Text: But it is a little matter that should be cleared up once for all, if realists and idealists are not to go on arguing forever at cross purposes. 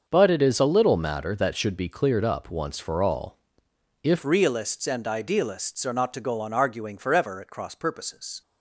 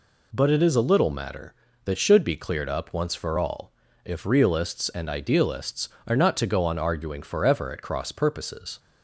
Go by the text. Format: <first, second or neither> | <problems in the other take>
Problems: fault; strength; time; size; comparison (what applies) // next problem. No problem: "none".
second | starts louder than the rest; until 1.0 s; 6.5 dB // changes voice at "realists"; from 4.2 s on; 4.2 s long